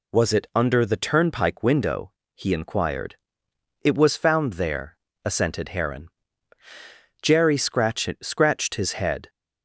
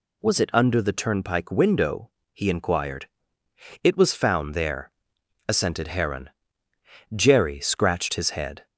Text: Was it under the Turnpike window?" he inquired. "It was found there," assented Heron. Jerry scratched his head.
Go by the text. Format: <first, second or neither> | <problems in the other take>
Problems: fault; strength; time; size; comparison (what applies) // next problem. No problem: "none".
second | says "scratched" twice; at 8.2 s